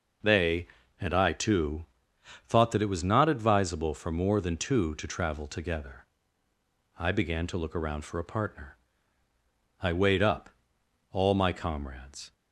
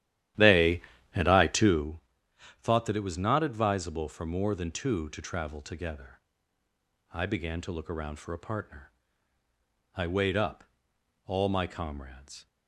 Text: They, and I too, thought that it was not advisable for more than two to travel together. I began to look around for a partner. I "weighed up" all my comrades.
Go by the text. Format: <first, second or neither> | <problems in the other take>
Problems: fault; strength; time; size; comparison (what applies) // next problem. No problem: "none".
first | starts louder than the rest; strong; until 1.9 s; 12 dB // pauses between "up" and "all"; noticeable; at 10.6 s; 0.64 s long; noticeable in the first